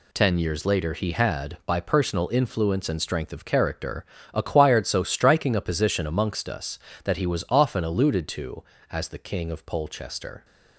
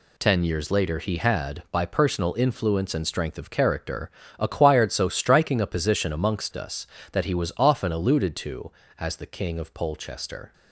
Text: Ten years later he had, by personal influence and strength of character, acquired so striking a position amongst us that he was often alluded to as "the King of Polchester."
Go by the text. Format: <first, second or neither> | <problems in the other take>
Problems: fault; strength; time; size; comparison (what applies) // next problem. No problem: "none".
neither | none